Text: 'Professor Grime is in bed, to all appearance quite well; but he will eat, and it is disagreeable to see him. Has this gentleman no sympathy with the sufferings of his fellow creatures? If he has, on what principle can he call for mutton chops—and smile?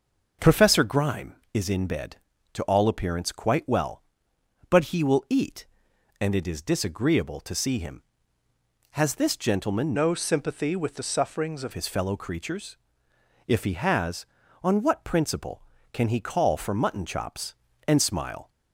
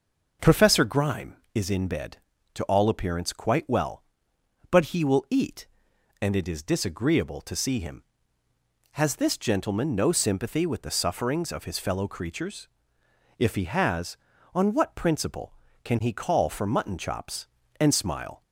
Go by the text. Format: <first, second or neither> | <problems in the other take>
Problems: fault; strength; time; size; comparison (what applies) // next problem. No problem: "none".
second | starts louder than the rest; noticeable; until 1.5 s; 6 dB // changes voice from "no" to "of"; from 9.9 to 11.7 s; 1.8 s long